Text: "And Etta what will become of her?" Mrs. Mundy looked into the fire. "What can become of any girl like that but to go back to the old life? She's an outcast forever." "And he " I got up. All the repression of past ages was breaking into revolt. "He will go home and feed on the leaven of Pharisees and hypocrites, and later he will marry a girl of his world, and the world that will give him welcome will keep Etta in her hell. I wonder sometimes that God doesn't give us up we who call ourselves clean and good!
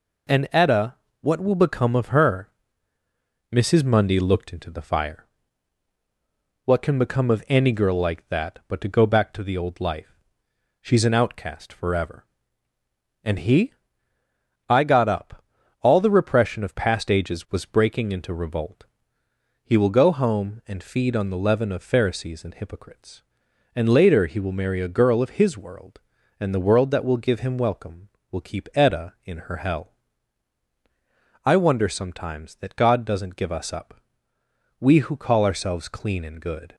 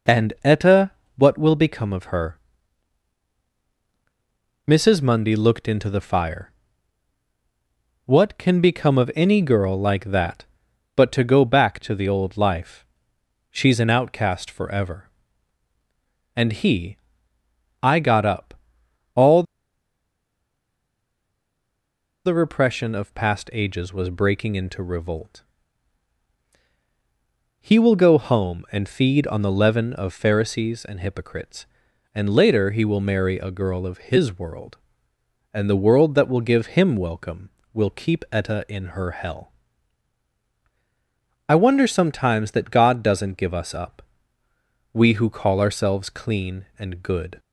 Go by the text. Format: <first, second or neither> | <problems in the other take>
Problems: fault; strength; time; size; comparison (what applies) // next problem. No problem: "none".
first | pauses between "Etta" and "what"; slight; at 0.9 s; 0.26 s long; slight in the first // pauses between "All" and "the"; strong; at 19.4 s; 2.8 s long // pauses between "up" and "we"; noticeable; at 44.0 s; 0.92 s long; noticeable in the first